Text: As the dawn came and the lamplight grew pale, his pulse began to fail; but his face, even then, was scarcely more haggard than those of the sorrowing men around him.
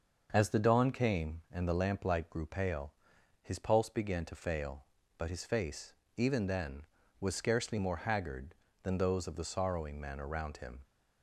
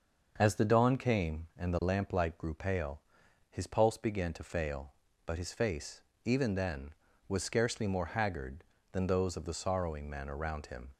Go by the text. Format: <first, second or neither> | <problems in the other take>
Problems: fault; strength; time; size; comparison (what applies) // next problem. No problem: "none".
neither | starts louder than the rest; the same in both